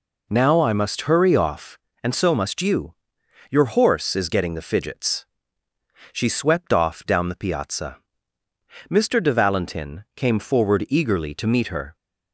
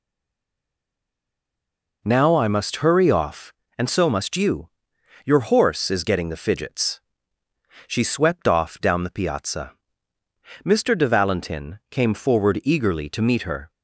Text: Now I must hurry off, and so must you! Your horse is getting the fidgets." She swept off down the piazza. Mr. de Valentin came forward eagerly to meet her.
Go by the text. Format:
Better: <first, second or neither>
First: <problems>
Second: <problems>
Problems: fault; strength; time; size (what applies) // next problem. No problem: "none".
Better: first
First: none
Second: stays silent before the first word; noticeable; until 2.0 s; 2.0 s long